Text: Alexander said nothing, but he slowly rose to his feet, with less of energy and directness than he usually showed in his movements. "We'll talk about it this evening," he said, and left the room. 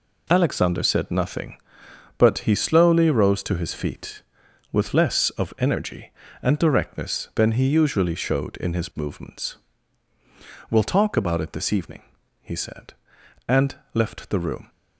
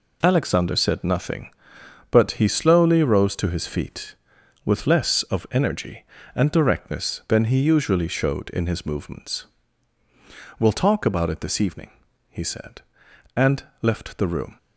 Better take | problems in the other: neither | pauses between "and" and "left"; slight; the same in both

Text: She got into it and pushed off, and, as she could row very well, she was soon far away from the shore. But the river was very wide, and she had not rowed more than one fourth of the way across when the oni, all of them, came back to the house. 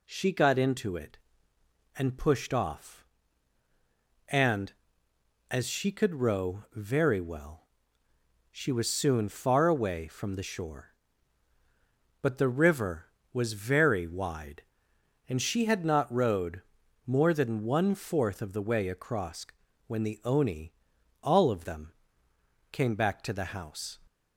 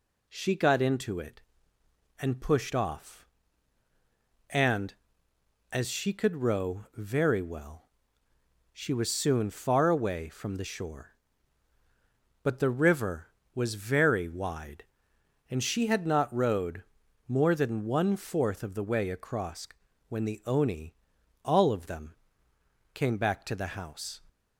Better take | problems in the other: neither | pauses between "rowed" and "more"; the same in both // pauses between "across" and "when"; the same in both

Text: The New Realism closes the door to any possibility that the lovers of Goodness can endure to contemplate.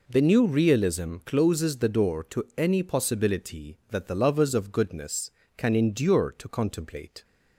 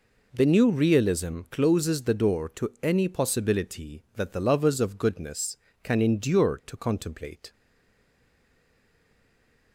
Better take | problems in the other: first | stays silent after the last word; from 7.5 s on; 2.2 s long

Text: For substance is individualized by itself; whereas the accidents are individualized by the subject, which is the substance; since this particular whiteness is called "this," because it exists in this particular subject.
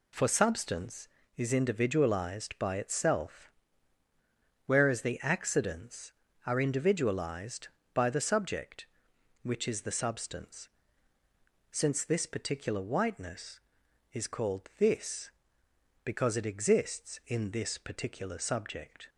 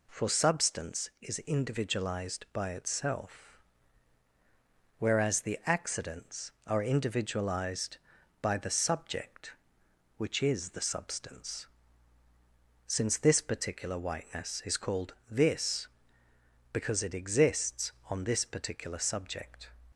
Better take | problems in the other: first | pauses between "called" and "this"; slight; at 15.1 s; 0.16 s long // says "on" for "in"; at 18.0 s

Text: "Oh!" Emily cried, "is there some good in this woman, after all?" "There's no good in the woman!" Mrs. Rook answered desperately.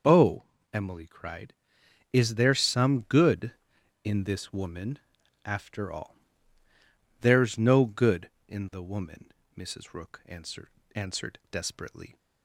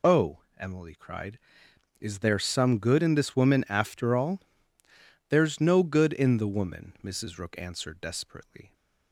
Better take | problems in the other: second | says "answered" twice; at 10.9 s

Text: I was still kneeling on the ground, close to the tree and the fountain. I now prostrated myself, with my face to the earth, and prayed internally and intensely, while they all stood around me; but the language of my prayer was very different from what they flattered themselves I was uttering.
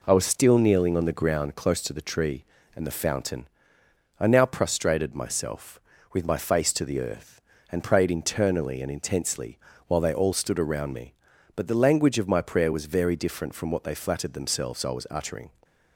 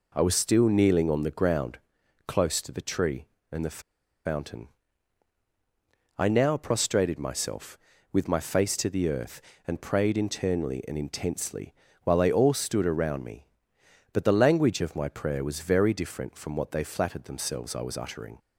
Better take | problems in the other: first | pauses between "the" and "fountain"; noticeable; at 3.7 s; 0.46 s long

